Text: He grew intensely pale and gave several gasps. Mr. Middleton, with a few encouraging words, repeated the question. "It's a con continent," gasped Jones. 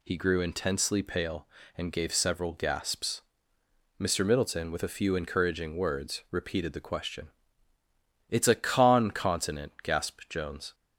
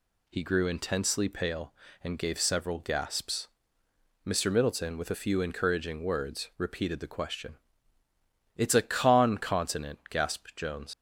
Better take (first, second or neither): first